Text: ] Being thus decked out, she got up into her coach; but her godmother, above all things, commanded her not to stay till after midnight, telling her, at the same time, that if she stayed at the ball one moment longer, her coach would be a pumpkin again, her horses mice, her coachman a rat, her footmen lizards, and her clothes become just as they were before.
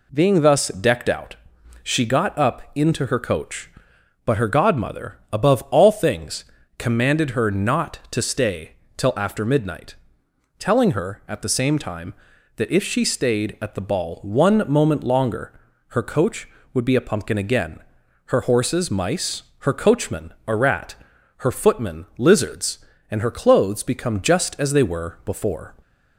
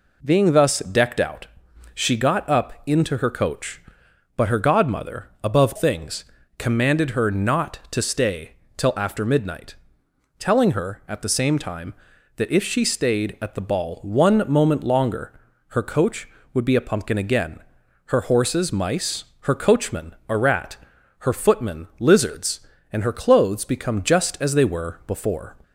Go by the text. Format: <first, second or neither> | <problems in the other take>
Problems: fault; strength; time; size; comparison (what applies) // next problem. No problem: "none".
first | skips "all"; at 5.7 s // pauses between "stay" and "till"; slight; at 8.5 s; 0.24 s long; slight in the first